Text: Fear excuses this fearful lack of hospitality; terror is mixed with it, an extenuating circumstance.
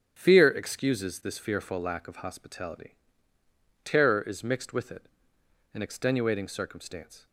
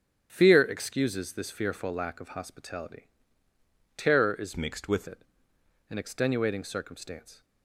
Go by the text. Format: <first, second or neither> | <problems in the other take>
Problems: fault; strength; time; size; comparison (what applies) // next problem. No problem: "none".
first | starts louder than the rest; strong; until 1.3 s; 9 dB; strong in the first // changes voice from "mixed" to "with"; from 4.5 to 5.0 s; 0.5 s long